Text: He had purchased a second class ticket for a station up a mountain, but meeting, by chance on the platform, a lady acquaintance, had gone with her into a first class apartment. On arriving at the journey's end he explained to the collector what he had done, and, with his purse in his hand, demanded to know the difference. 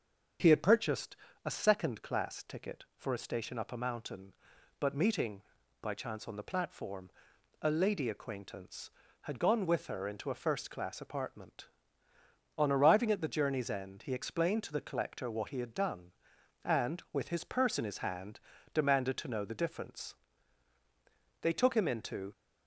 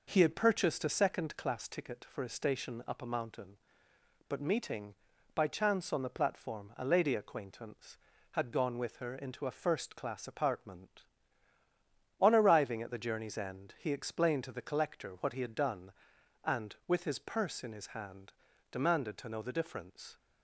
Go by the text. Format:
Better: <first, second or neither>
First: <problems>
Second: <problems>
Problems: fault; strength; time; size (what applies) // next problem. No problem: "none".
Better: second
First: starts louder than the rest; until 1.7 s; 7 dB // pauses between "purchased" and "a"; slight; at 1.1 s; 0.30 s long // goes on to say "They took him into"; noticeable; from 21.4 s on; 0.90 s long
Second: none